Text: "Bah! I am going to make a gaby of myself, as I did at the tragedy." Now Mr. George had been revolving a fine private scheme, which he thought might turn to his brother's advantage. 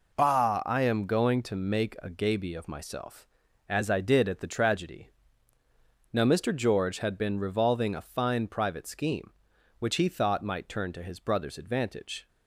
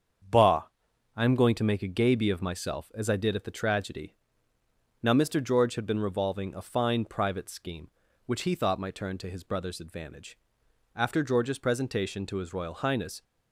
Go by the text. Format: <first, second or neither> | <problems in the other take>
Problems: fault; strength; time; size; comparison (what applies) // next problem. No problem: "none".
first | starts louder than the rest; strong; until 1.8 s; 7.5 dB // goes on to say "After George's presentation to his Royal Highness"; strong; from 10.9 s on; 2.2 s long